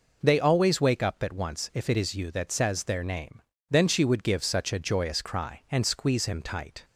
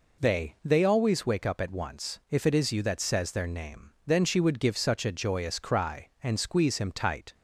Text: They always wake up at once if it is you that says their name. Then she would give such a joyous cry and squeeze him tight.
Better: first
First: none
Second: says "They" twice; at 0.6 s

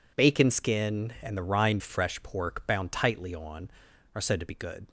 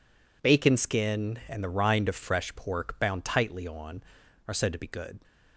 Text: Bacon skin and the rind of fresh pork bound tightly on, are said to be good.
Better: second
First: skips "of"; at 1.8 s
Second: none

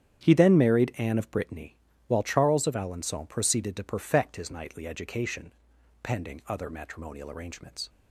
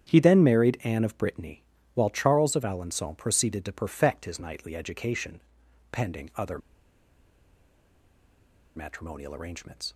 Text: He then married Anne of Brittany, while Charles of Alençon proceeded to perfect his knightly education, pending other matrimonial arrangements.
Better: first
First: starts louder than the rest; strong; until 1.3 s; 9.5 dB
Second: starts louder than the rest; strong; until 1.1 s; 9.5 dB // pauses between "other" and "matrimonial"; strong; at 6.5 s; 2.1 s long

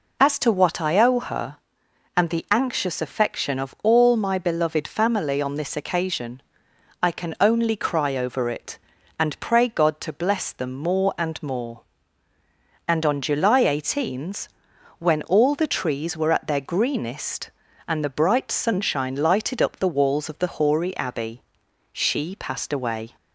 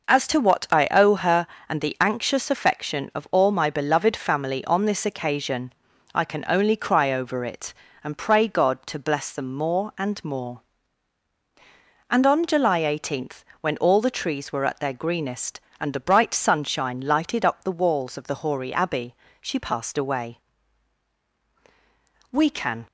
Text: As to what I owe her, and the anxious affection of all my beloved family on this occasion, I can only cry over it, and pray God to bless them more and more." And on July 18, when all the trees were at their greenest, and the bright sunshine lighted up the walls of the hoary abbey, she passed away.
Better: first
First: none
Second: goes on to say "We can"; from 22.3 s on; 0.56 s long

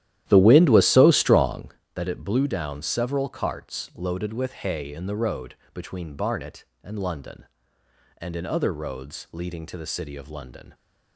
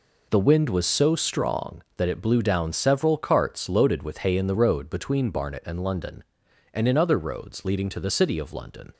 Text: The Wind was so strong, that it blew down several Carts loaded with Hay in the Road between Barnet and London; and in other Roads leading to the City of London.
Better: second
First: starts louder than the rest; strong; until 1.8 s; 13 dB // pauses between "Road" and "between"; slight; at 5.5 s; 0.18 s long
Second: none

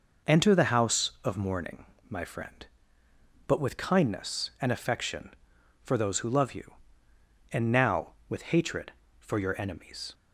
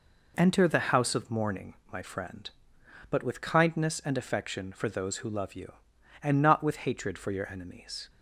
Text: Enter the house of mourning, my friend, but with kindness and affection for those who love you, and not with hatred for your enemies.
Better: second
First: says "now" for "not"; at 7.7 s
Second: none

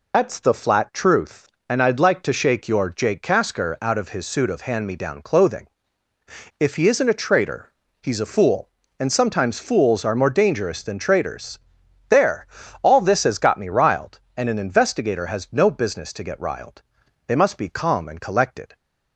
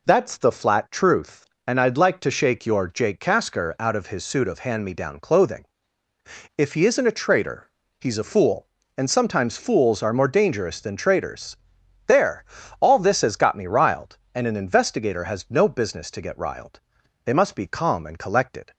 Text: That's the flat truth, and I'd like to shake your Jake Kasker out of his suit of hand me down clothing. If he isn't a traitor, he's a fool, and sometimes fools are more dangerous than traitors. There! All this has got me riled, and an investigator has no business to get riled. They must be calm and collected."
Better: second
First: loses the start of "That's"; at 0.1 s; 65 ms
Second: none

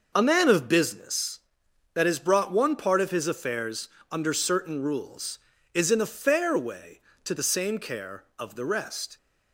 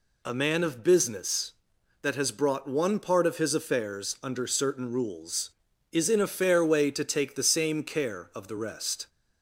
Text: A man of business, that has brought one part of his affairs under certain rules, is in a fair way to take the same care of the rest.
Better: second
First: pauses between "affairs" and "under"; slight; at 3.8 s; 0.22 s long // skips "take"; at 7.3 s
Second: none

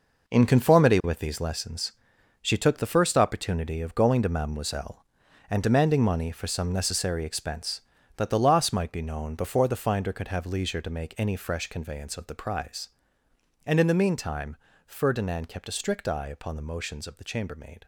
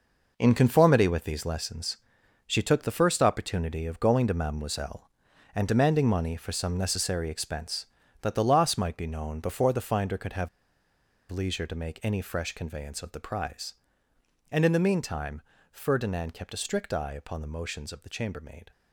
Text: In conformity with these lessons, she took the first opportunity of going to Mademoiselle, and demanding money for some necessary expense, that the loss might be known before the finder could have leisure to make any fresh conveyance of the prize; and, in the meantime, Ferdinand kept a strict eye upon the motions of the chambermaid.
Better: first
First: none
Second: pauses between "have" and "leisure"; noticeable; at 10.4 s; 0.81 s long

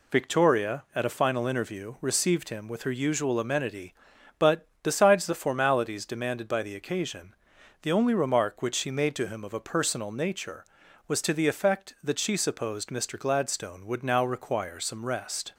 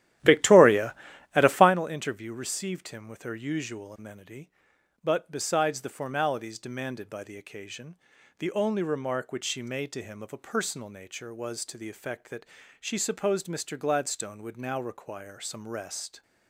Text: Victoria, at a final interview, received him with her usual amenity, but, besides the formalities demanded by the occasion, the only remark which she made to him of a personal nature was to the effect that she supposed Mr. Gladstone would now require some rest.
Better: first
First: none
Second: starts louder than the rest; strong; until 1.7 s; 13.5 dB // pauses between "that" and "she"; slight; at 12.4 s; 0.34 s long

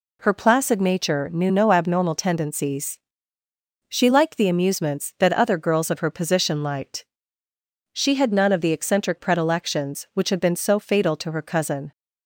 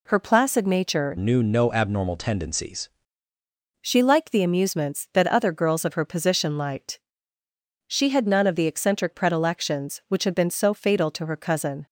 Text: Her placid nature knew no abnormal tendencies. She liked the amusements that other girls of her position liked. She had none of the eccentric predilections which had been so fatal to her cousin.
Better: first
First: none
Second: changes voice from "knew" to "tendencies"; from 1.1 to 2.8 s; 1.7 s long

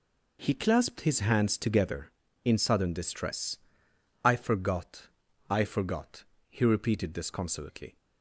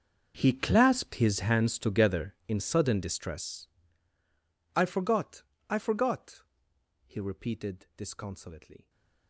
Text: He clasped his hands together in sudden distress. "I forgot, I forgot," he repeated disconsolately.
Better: first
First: none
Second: gets quieter; strong; throughout; 20 dB

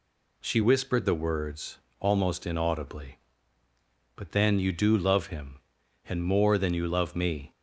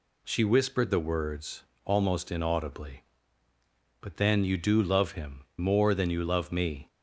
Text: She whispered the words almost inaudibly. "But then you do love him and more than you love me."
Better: first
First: pauses between "words" and "almost"; slight; at 1.7 s; 0.24 s long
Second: pauses between "words" and "almost"; slight; at 1.6 s; 0.24 s long // skips "and"; at 5.5 s

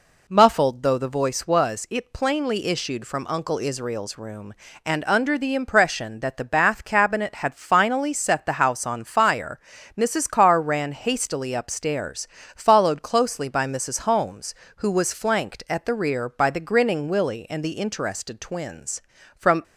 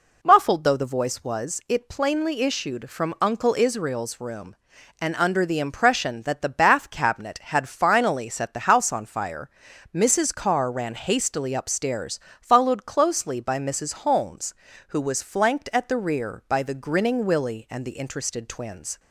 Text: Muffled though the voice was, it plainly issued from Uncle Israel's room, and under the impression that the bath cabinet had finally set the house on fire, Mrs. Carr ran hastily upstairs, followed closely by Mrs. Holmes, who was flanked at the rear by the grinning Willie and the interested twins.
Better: second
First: goes on to say "From"; slight; from 19.3 s on; 0.26 s long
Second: none

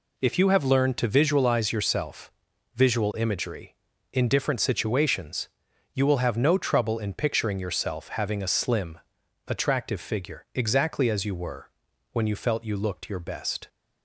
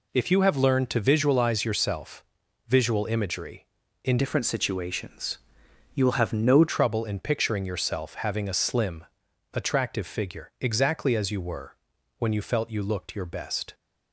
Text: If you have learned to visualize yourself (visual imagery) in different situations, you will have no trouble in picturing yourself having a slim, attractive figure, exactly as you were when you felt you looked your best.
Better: first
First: pauses between "were" and "when"; at 11.6 s; 0.44 s long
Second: changes voice from "different" to "no"; from 4.1 to 6.6 s; 2.5 s long // pauses between "were" and "when"; at 11.7 s; 0.44 s long

